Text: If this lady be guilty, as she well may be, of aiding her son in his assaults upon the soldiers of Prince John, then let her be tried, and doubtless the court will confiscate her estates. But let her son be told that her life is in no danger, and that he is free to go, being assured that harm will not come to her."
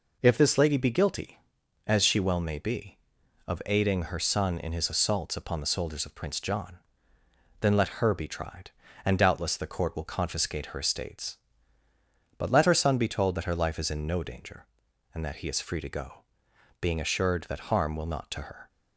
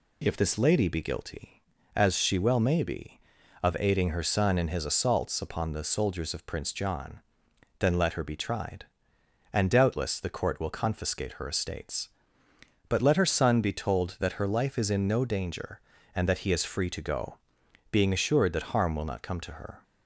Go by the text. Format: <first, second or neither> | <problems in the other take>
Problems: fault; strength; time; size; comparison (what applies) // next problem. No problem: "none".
second | skips "come"; at 18.3 s